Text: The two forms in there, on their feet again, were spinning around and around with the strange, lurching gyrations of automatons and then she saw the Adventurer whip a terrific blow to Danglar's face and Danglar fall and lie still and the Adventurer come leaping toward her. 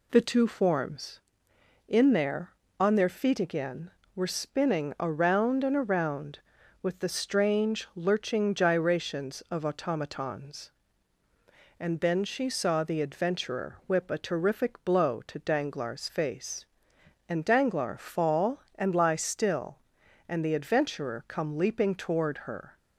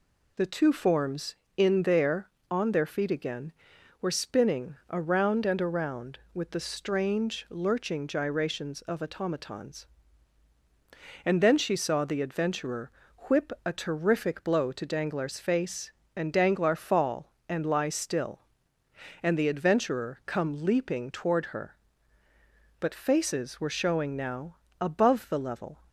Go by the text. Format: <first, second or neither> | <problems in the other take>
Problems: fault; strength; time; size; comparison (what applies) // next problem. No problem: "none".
first | pauses between "Adventurer" and "whip"; at 12.8 s; 0.40 s long // goes on to say "But faces were showing now above the level"; strong; from 22.7 s on; 3.0 s long